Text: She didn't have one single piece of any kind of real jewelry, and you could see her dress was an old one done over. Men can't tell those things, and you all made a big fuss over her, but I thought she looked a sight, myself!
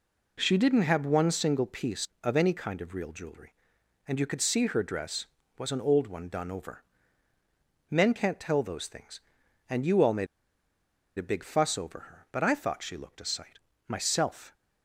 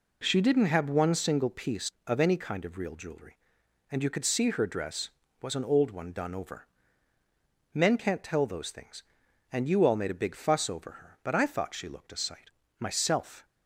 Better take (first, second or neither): second